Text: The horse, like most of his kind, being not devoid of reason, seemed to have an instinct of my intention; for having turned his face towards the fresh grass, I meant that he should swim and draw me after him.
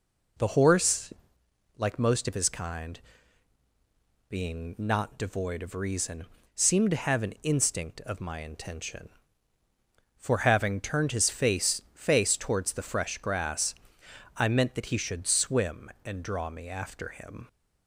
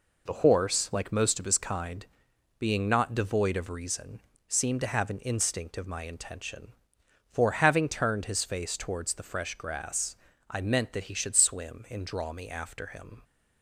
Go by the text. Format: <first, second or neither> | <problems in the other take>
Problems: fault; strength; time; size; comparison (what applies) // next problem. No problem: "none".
second | says "face" twice; at 11.9 s